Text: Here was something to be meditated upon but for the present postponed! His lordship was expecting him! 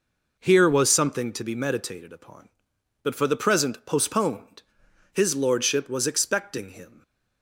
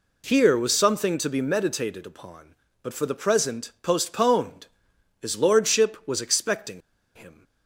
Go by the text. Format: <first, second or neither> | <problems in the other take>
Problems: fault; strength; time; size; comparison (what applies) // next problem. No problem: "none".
first | pauses between "expecting" and "him"; slight; at 6.8 s; 0.34 s long